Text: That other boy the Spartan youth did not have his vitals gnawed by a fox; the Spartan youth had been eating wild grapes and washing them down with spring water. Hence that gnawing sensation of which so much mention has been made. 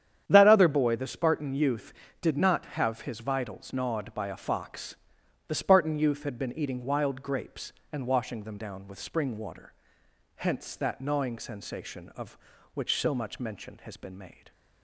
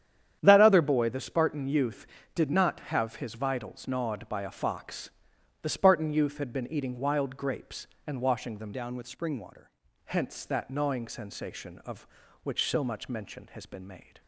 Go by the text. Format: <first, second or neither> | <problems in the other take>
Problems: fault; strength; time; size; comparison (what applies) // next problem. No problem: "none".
first | starts louder than the rest; strong; until 1.4 s; 9.5 dB; strong in the first // changes voice from "down" to "water"; from 8.7 to 9.6 s; 0.9 s long